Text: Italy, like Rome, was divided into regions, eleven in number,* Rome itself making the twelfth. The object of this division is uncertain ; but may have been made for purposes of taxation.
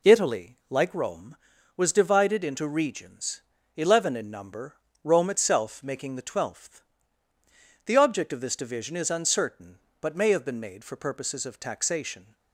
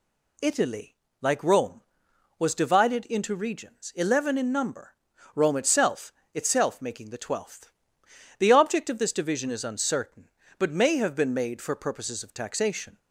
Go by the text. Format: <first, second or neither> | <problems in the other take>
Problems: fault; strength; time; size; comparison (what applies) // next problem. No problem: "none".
first | says "itself" twice; at 6.3 s